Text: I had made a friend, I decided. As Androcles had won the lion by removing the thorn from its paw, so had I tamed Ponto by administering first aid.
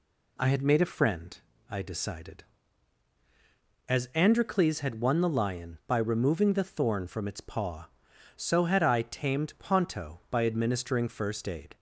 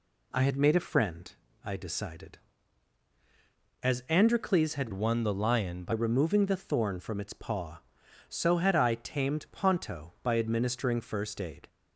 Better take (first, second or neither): first